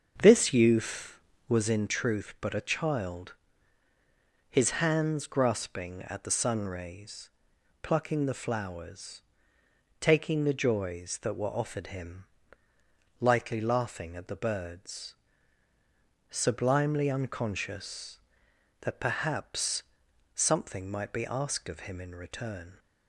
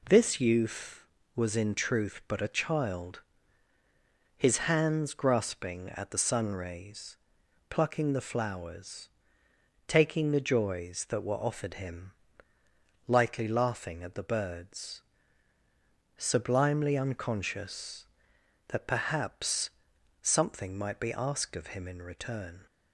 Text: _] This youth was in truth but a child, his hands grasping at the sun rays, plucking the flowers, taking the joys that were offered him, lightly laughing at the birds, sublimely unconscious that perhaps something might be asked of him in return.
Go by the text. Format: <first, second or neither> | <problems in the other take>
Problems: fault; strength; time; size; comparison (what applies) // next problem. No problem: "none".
second | starts louder than the rest; until 1.9 s; 6.5 dB // pauses between "perhaps" and "something"; noticeable; at 19.8 s; 0.50 s long; noticeable in the second